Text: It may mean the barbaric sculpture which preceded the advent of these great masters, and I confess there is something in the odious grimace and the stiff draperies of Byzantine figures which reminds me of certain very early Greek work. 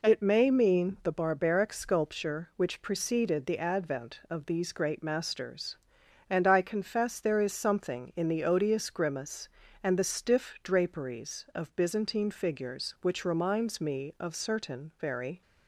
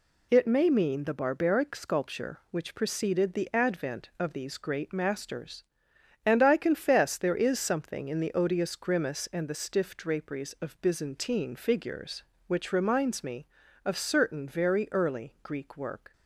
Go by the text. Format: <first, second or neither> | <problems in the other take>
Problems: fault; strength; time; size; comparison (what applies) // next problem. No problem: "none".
second | stops before "early Greek work"; at 15.4 s